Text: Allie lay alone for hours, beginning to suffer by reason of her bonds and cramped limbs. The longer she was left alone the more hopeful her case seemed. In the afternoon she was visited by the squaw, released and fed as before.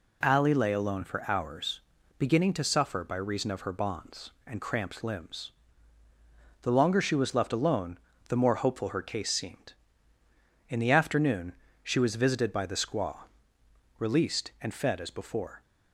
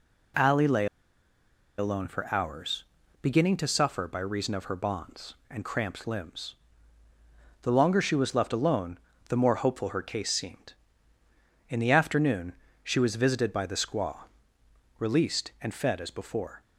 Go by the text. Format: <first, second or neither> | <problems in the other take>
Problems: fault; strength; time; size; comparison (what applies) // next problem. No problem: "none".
first | pauses between "lay" and "alone"; noticeable; at 0.8 s; 0.93 s long // pauses between "alone" and "the"; slight; at 8.9 s; 0.30 s long; slight in the first // pauses between "afternoon" and "she"; slight; at 12.5 s; 0.30 s long; slight in the first